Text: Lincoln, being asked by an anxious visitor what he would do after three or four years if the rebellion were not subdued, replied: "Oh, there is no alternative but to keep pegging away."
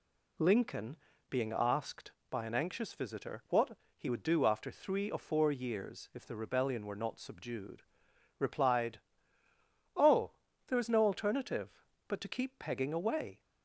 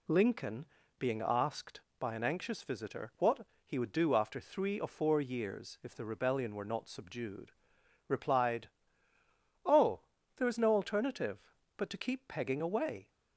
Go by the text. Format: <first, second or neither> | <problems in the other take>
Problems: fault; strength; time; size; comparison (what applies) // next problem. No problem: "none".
neither | pauses between "what" and "he"; slight; the same in both